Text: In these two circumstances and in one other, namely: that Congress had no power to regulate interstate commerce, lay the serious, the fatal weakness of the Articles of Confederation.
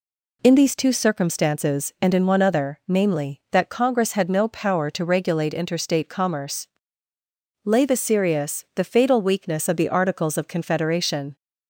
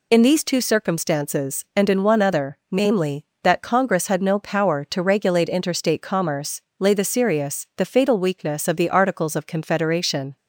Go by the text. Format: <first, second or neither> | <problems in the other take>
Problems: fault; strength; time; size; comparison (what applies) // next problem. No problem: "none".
neither | none